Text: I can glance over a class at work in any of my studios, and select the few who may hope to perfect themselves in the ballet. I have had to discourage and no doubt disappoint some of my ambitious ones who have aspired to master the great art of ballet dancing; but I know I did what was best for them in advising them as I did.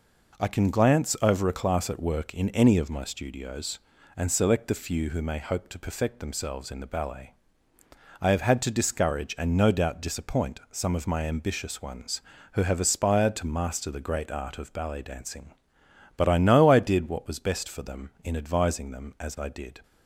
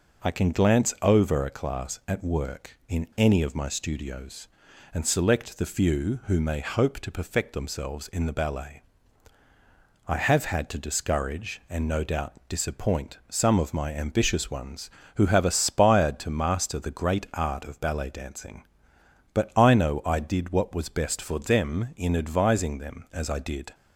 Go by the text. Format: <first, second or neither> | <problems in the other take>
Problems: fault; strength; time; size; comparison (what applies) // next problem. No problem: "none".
neither | none